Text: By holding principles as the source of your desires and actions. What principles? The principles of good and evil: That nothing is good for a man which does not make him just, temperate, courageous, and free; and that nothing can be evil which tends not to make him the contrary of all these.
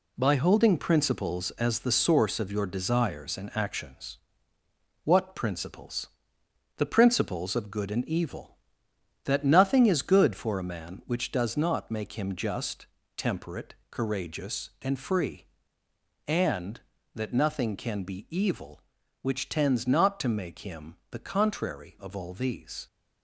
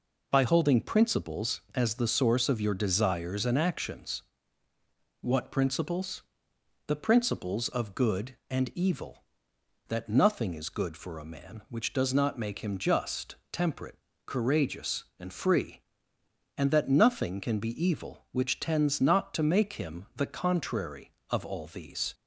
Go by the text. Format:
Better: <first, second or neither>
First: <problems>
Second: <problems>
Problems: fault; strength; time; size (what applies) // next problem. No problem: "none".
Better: second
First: gets quieter; throughout; 6 dB // pauses between "him" and "the"; slight; at 20.9 s; 0.16 s long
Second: none